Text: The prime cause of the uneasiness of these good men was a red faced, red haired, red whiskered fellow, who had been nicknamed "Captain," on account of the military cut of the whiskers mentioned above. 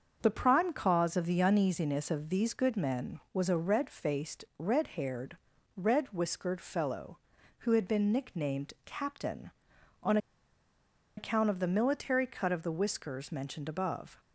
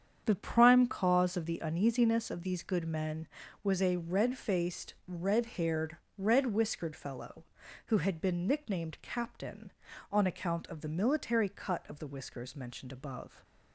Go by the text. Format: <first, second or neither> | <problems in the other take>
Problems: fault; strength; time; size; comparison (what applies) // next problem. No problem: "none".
second | starts louder than the rest; until 1.2 s; 6.5 dB; strong in the second // pauses between "on" and "account"; at 10.1 s; 1.0 s long